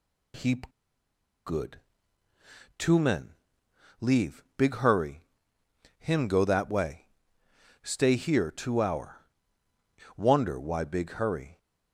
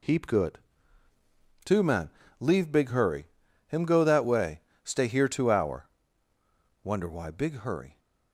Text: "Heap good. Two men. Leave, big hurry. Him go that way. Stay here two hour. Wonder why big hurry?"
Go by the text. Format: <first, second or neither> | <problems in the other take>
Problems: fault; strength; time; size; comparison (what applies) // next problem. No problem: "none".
second | pauses between "Heap" and "good"; noticeable; at 0.6 s; 0.76 s long